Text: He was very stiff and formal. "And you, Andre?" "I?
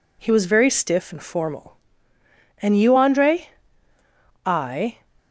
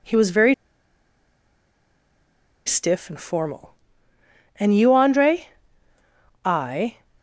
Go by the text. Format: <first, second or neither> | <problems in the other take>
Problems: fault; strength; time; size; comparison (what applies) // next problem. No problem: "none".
first | pauses between "very" and "stiff"; strong; at 0.5 s; 2.1 s long